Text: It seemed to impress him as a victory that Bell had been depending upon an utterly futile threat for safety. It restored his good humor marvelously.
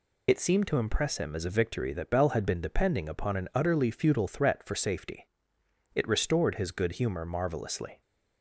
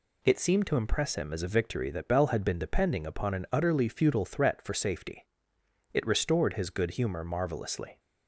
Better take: second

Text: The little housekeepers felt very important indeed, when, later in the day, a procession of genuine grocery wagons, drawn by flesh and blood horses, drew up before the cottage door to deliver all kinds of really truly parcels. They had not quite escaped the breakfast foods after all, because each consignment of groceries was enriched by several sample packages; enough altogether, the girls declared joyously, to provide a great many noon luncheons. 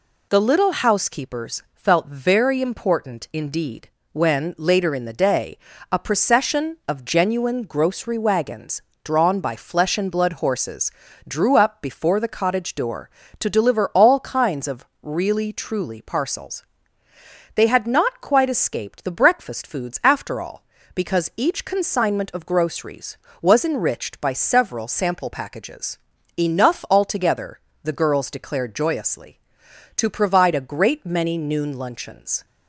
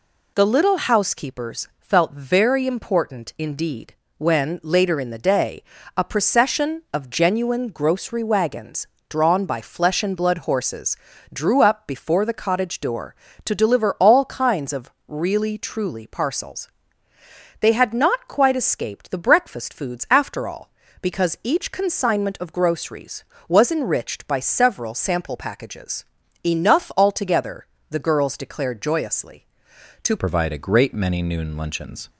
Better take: first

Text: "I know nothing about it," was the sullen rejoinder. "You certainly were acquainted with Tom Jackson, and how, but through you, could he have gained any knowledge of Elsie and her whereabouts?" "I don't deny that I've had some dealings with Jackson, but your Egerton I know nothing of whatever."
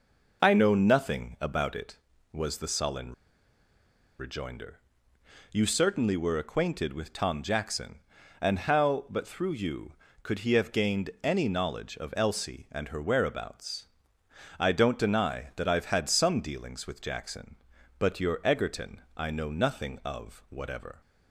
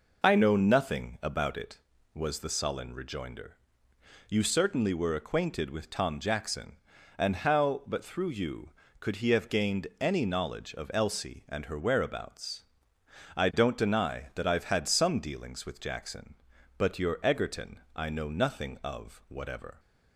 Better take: second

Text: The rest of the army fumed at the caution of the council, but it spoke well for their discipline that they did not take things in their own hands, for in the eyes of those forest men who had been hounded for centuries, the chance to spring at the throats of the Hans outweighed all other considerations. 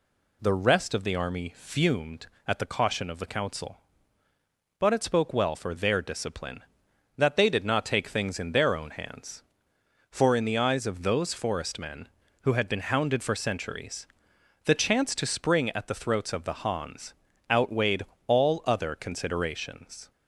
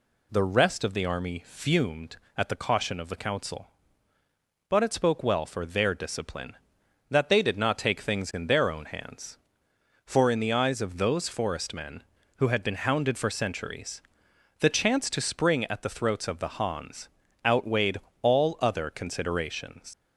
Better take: first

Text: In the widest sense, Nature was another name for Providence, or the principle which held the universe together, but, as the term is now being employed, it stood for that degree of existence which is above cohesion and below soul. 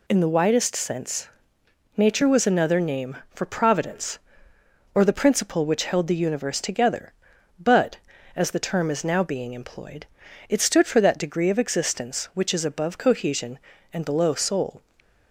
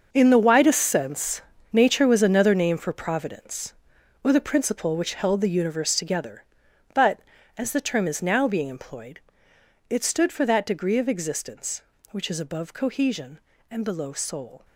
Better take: first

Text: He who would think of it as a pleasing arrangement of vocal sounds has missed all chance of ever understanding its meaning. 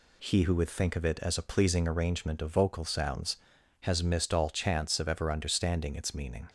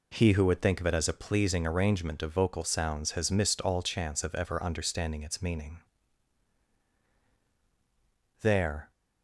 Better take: first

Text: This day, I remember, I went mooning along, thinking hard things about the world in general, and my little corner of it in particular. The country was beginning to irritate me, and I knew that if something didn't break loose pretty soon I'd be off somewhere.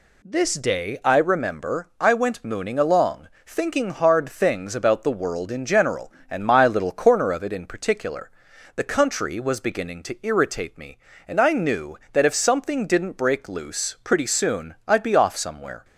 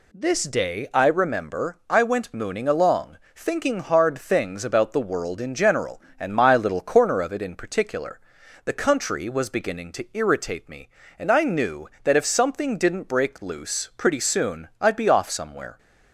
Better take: neither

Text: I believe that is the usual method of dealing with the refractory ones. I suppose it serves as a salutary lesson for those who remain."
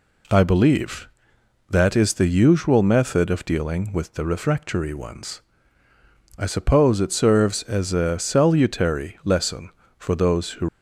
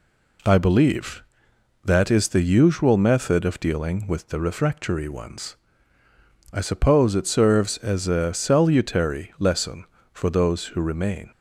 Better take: second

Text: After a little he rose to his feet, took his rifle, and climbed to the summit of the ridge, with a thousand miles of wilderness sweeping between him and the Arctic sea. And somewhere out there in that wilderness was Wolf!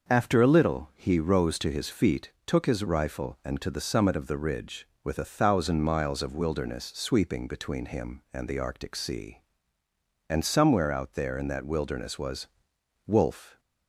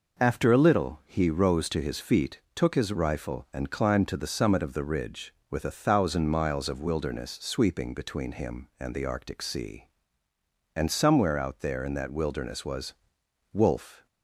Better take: second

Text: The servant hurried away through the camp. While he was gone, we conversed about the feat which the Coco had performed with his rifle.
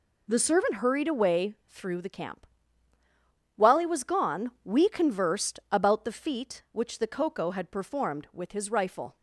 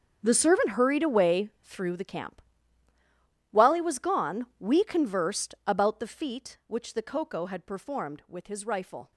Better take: first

